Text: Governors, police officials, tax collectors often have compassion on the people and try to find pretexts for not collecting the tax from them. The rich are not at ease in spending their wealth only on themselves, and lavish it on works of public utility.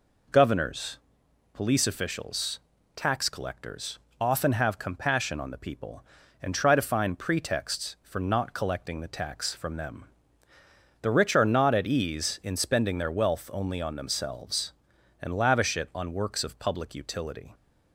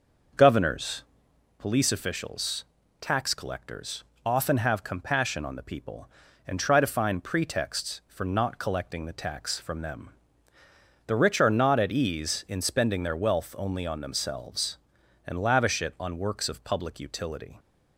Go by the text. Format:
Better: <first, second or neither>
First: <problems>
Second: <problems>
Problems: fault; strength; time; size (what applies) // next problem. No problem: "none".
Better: first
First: pauses between "collectors" and "often"; slight; at 3.9 s; 0.22 s long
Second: starts louder than the rest; noticeable; until 1.6 s; 6 dB // pauses between "collectors" and "often"; slight; at 4.0 s; 0.22 s long